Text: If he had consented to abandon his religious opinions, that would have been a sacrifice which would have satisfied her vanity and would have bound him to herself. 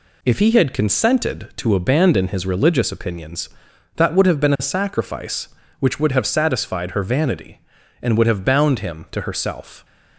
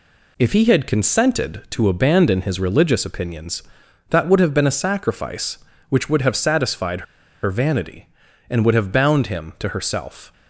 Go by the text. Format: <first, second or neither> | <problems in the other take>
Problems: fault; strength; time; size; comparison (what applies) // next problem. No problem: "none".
first | pauses between "satisfied" and "her"; at 7.0 s; 0.40 s long